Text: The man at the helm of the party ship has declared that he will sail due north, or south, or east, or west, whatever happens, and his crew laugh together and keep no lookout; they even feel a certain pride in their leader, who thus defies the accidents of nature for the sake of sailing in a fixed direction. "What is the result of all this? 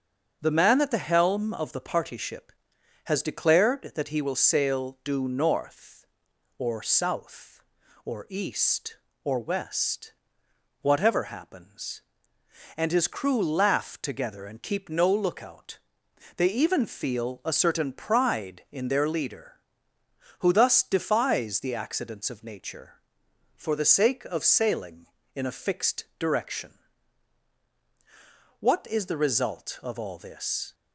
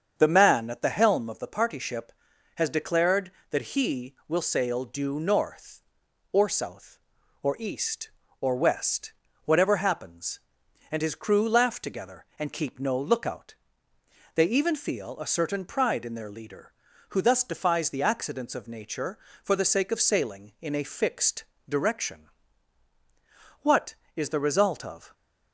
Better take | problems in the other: first | starts louder than the rest; strong; until 1.1 s; 7 dB; also in the first // pauses between "fixed" and "direction"; slight; at 21.4 s; 0.26 s long; slight in the first // stops before "all this"; at 25.1 s

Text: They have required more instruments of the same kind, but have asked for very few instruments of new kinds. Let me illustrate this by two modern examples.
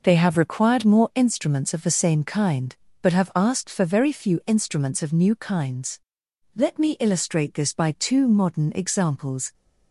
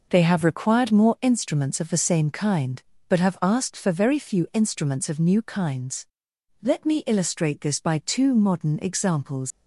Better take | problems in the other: first | leaves "examples" unfinished; at 9.5 s; 95 ms

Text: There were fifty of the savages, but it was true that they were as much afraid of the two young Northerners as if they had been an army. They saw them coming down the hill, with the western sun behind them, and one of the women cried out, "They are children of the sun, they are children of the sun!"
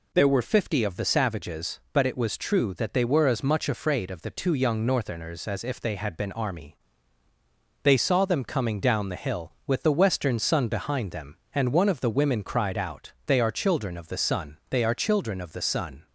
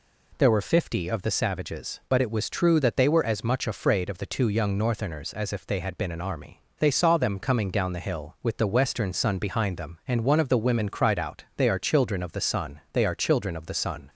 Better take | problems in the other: second | skips "an"; at 6.3 s

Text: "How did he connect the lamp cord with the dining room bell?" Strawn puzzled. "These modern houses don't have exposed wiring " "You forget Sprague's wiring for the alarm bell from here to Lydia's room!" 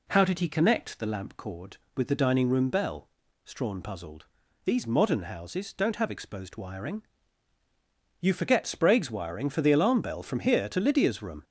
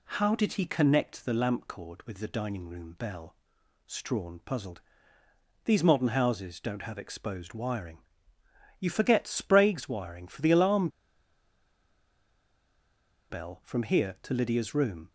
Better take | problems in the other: first | pauses between "alarm" and "bell"; strong; at 10.8 s; 2.4 s long

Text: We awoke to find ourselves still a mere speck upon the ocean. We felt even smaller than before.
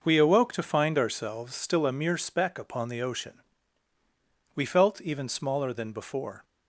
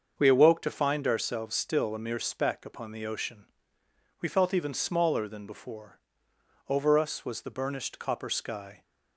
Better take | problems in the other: first | starts louder than the rest; until 1.1 s; 6.5 dB // goes on to say "Over us was the burnished copper sky"; strong; from 6.6 s on; 2.1 s long

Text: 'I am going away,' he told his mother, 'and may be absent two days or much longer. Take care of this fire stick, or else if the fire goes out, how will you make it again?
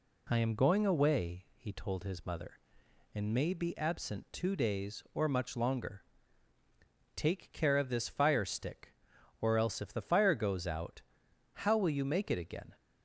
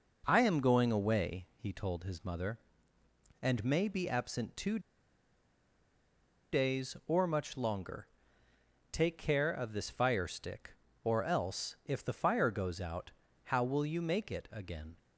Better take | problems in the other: first | pauses between "two" and "days"; strong; at 4.7 s; 1.7 s long

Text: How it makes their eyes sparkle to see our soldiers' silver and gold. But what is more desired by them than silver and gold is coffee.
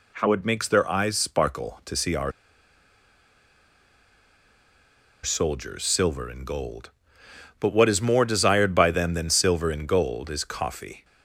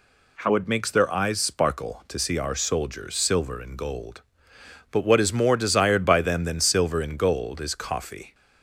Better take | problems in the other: second | pauses between "our" and "soldiers"; strong; at 2.3 s; 2.9 s long

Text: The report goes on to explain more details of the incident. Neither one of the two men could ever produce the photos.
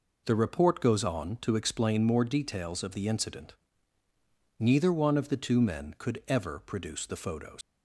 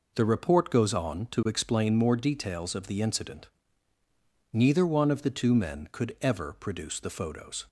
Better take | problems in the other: second | leaves "photos" unfinished; at 7.6 s; 125 ms

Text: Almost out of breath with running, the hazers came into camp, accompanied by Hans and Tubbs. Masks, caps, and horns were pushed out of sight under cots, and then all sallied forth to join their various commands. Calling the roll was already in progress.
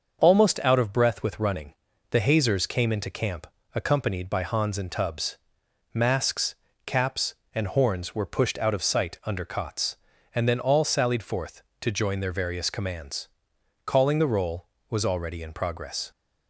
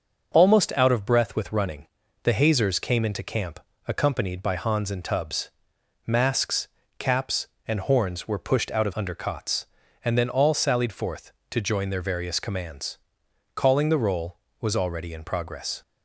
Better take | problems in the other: first | starts louder than the rest; until 1.3 s; 6.5 dB; also in the first // skips "sight"; at 8.9 s

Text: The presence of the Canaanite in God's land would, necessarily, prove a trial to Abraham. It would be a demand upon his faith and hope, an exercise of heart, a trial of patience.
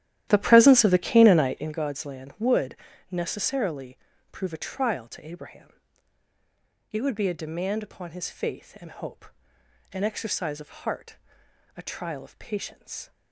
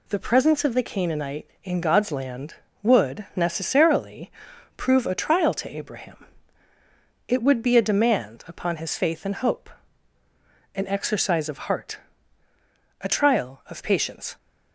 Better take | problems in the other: second | starts louder than the rest; strong; until 1.8 s; 12.5 dB

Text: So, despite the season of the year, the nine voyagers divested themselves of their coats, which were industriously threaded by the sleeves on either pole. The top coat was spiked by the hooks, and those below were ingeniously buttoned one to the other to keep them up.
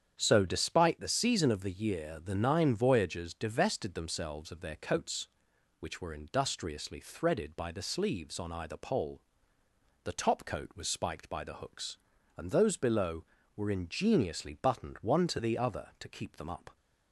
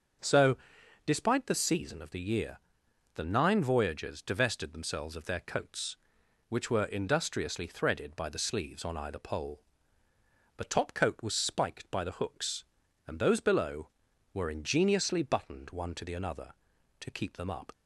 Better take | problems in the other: first | starts louder than the rest; until 1.6 s; 7 dB; strong in the first // says "another" for "other"; at 16.1 s

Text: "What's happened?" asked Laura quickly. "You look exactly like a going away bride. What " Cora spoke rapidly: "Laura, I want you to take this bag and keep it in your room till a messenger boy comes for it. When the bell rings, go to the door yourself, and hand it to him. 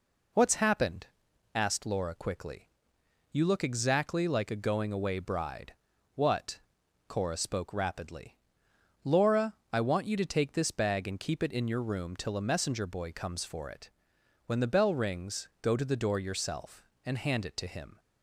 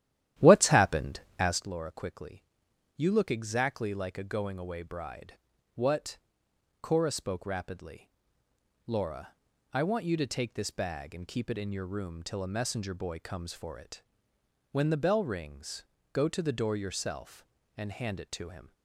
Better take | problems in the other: first | starts louder than the rest; strong; until 1.7 s; 12 dB

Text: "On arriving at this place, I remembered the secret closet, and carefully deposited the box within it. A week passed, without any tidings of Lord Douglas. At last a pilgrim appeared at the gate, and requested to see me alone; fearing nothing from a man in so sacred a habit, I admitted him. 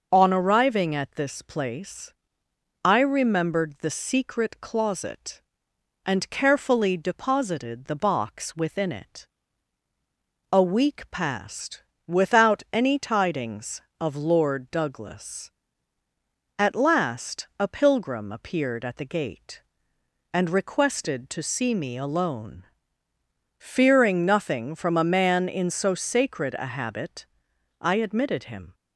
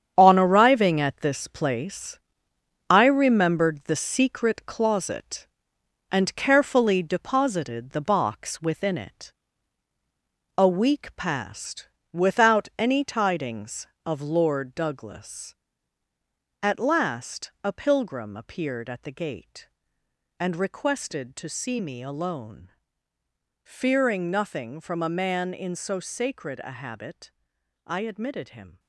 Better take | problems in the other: first | gets quieter; strong; throughout; 9.5 dB // starts louder than the rest; strong; until 1.1 s; 8.5 dB; noticeable in the first

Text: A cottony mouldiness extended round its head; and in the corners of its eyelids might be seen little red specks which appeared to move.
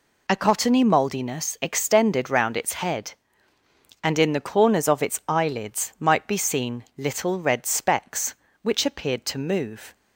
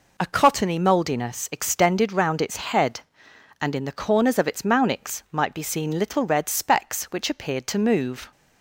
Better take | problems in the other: first | says "mounix" for "eyelids"; at 4.6 s

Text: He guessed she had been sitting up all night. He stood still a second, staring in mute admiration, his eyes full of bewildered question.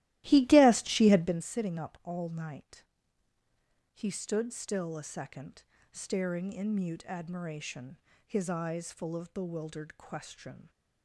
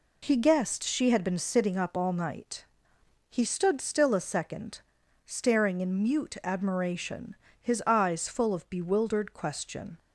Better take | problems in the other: second | starts louder than the rest; strong; until 1.4 s; 15.5 dB

